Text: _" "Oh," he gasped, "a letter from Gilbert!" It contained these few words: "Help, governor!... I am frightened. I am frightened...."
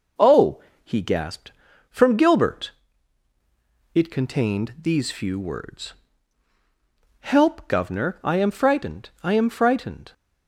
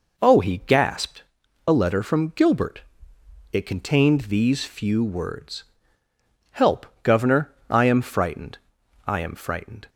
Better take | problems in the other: second | skips "a letter"; at 1.7 s

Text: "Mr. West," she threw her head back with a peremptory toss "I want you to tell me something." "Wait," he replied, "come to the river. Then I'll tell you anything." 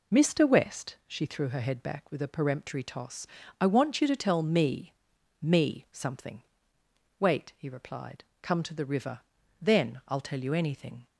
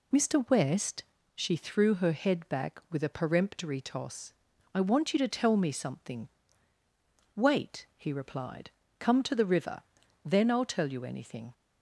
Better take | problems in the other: second | pauses between "toss" and "I"; slight; at 3.2 s; 0.34 s long; also in the second // says "me" twice; at 5.4 s

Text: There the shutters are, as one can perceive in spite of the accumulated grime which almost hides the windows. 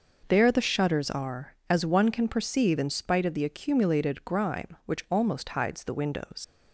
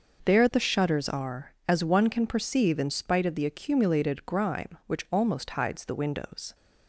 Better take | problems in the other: second | leaves "windows" unfinished; at 6.4 s; 90 ms

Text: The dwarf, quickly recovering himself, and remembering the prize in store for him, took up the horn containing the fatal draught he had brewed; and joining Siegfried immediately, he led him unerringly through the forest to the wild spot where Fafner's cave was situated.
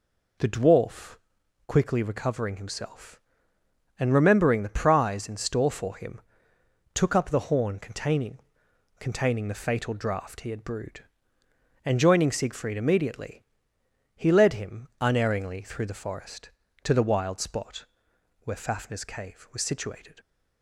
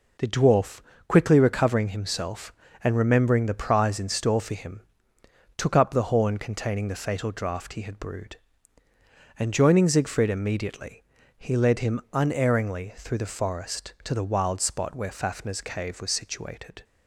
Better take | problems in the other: second | says "containing" twice; at 8.9 s // pauses between "spot" and "where"; noticeable; at 17.8 s; 0.56 s long

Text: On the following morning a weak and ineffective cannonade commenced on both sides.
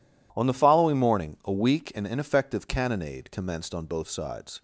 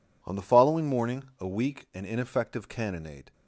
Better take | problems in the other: first | pauses between "morning" and "a"; slight; at 1.2 s; 0.16 s long // stops before "commenced on both sides"; at 3.3 s

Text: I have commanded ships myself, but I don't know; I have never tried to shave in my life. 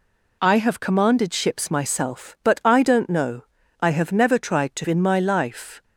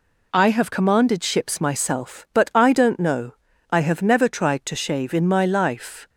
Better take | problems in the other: second | skips "shave"; at 4.8 s

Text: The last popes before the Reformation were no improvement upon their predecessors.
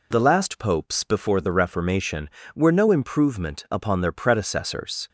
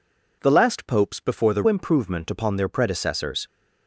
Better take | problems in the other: first | skips "Reformation were no"; at 1.6 s

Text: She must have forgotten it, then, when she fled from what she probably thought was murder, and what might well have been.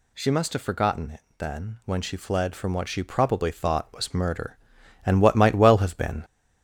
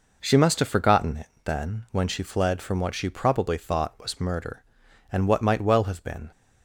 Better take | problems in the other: second | gets louder; noticeable; throughout; 4 dB

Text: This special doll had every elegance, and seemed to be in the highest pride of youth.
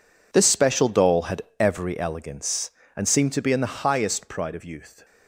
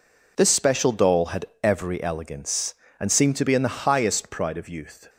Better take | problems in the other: second | gets quieter; strong; throughout; 15.5 dB // pauses between "had" and "every"; slight; at 1.4 s; 0.18 s long; slight in the second

